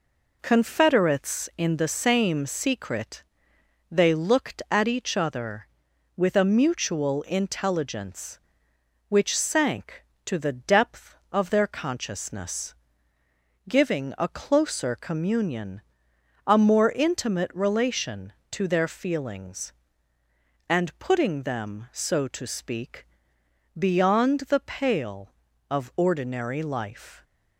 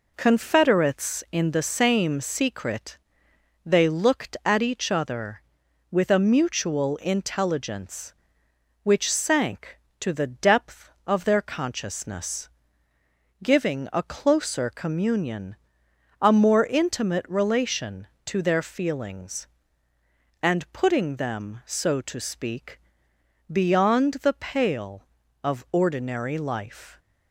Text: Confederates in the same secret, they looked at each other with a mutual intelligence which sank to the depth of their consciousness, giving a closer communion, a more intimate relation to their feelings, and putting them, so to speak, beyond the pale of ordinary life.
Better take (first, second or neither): neither